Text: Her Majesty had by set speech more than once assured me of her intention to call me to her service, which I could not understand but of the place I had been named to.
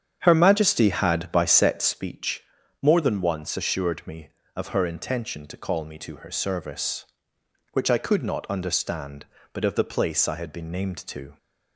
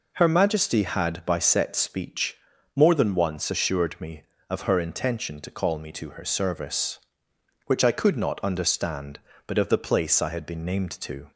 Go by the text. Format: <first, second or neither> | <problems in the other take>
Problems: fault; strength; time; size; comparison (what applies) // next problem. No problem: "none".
second | starts louder than the rest; strong; until 2.1 s; 8.5 dB // pauses between "speech" and "more"; at 2.4 s; 0.38 s long; also in the second